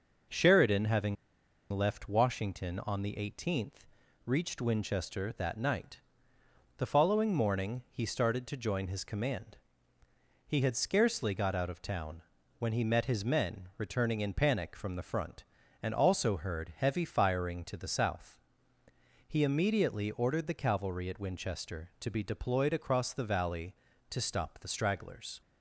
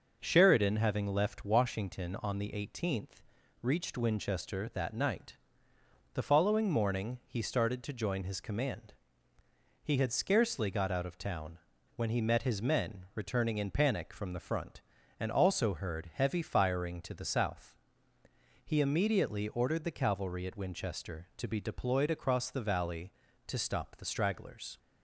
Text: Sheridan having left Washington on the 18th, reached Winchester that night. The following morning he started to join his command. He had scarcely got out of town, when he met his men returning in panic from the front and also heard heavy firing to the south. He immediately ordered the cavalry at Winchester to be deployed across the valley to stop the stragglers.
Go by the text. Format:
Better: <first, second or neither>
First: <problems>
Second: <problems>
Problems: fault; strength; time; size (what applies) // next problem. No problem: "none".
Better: second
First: pauses between "having" and "left"; noticeable; at 1.1 s; 0.55 s long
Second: none